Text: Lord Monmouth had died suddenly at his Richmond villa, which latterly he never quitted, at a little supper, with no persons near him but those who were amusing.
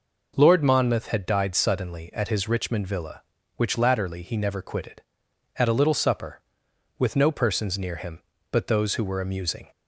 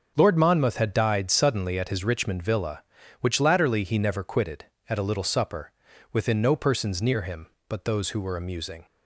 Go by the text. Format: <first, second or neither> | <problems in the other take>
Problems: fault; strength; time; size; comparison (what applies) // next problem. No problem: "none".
first | starts louder than the rest; until 1.1 s; 7 dB // says "within" for "with"; at 6.1 s